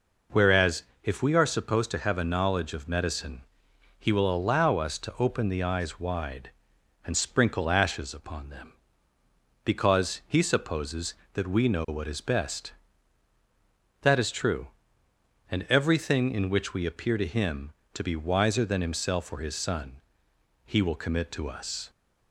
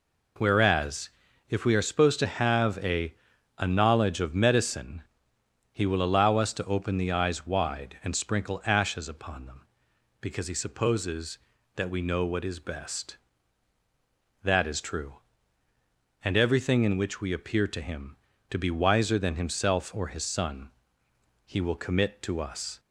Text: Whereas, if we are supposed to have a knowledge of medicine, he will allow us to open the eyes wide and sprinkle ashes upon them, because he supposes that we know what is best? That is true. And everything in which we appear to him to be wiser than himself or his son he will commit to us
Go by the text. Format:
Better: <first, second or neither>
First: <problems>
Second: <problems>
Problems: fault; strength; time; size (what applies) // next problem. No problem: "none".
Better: first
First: pauses between "son" and "he"; noticeable; at 19.9 s; 0.68 s long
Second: says "a" twice; at 3.5 s // pauses between "son" and "he"; noticeable; at 20.6 s; 0.78 s long